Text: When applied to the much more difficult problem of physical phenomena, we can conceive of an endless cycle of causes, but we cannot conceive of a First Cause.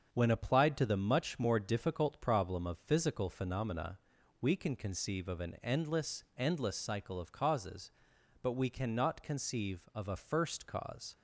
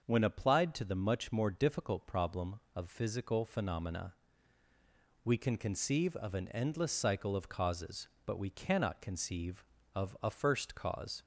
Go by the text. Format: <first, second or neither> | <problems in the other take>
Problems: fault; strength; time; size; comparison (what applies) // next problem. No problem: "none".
second | starts louder than the rest; until 1.1 s; 6.5 dB; also in the second // says "endless" twice; at 6.3 s